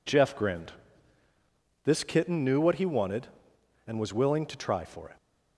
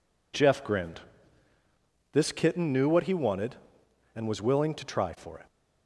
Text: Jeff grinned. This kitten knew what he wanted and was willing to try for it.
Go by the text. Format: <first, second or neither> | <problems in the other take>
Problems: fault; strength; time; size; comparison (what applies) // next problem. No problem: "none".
neither | none